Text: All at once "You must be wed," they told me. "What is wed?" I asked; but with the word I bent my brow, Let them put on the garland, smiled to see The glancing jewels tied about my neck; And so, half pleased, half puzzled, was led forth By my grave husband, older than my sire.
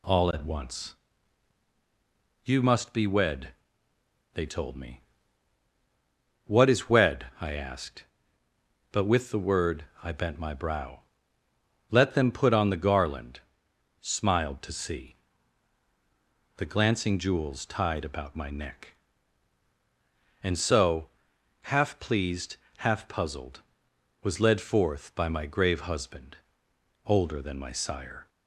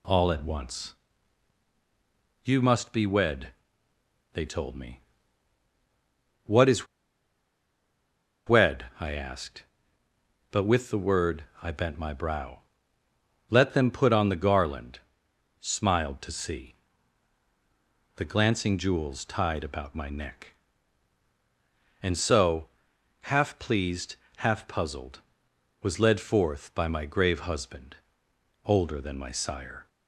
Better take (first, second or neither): first